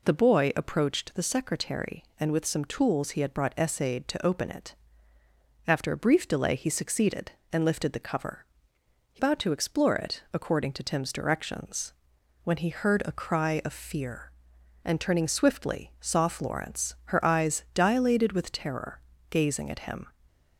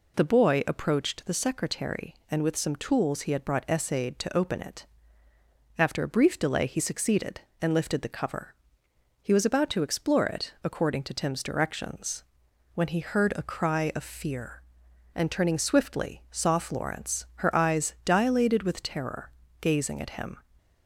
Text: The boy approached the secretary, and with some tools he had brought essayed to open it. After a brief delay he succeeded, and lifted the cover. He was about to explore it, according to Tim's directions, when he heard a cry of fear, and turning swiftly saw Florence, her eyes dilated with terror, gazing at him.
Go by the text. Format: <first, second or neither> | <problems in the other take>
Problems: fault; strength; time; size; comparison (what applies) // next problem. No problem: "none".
second | skips "was"; at 9.1 s // stays silent after the last word; slight; from 20.0 s on; 0.5 s long